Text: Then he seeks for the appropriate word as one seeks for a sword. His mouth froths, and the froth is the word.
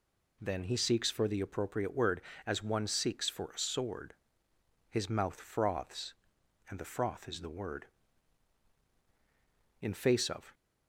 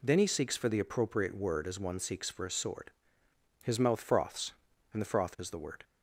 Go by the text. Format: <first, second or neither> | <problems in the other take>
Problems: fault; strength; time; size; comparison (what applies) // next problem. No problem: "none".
second | goes on to say "In face of"; noticeable; from 9.8 s on; 0.73 s long